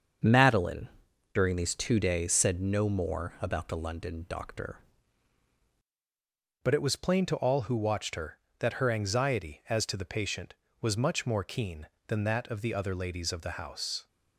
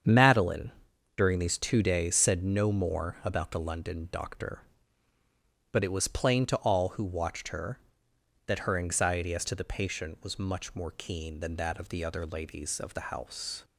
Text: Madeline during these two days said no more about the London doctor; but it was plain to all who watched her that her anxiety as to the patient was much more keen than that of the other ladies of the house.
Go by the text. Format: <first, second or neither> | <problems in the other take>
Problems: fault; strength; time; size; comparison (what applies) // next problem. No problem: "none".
second | starts louder than the rest; until 1.7 s; 6.5 dB; strong in the second // pauses between "Madeline" and "during"; noticeable; at 0.8 s; 0.48 s long; noticeable in the second // changes voice at "but"; from 6.6 s on; 7.4 s long